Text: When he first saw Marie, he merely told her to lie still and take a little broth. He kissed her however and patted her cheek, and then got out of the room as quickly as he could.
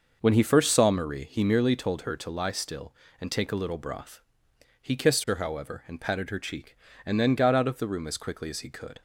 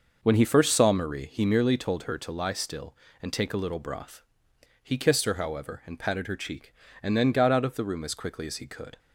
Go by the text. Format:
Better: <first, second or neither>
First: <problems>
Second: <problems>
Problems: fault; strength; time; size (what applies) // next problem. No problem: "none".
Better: neither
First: none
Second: none